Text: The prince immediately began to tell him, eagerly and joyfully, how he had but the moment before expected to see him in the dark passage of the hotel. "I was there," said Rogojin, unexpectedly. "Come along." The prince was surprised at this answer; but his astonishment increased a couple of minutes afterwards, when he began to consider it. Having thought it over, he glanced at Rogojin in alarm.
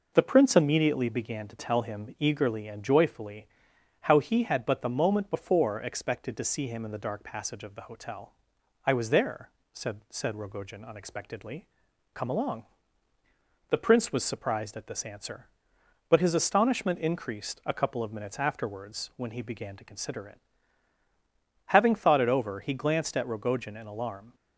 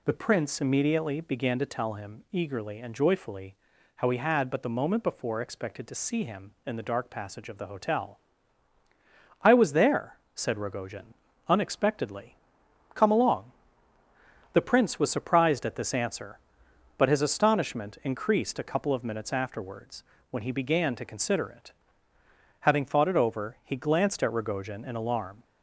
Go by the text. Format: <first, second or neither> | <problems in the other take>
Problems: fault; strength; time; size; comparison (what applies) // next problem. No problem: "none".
second | says "said" twice; at 10.1 s